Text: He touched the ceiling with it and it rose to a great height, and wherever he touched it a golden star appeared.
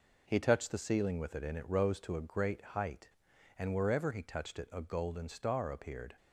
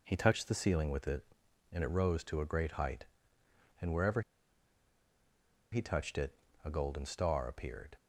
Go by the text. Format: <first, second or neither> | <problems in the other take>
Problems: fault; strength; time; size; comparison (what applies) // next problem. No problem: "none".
first | pauses between "wherever" and "he"; strong; at 4.2 s; 1.5 s long // pauses between "it" and "a"; slight; at 6.3 s; 0.30 s long